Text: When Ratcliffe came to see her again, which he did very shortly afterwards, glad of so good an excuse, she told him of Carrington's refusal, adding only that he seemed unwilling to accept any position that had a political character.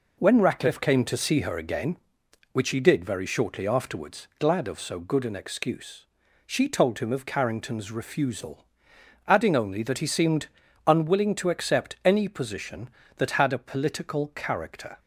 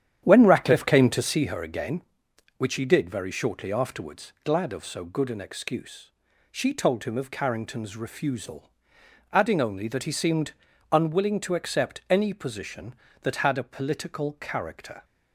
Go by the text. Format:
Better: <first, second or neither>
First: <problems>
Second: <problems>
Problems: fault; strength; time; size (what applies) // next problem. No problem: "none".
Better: first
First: pauses between "seemed" and "unwilling"; at 10.4 s; 0.38 s long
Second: starts louder than the rest; strong; until 1.4 s; 10 dB // pauses between "seemed" and "unwilling"; at 10.5 s; 0.38 s long